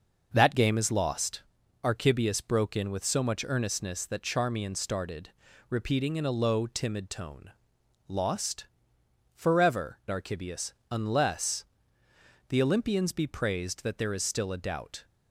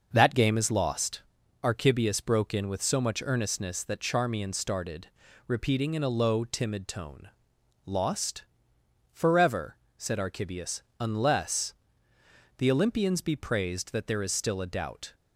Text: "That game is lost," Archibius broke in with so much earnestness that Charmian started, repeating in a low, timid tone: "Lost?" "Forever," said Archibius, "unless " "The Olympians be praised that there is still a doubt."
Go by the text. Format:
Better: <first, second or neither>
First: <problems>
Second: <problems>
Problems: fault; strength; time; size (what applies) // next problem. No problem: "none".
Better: second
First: skips "said"; at 10.0 s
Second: none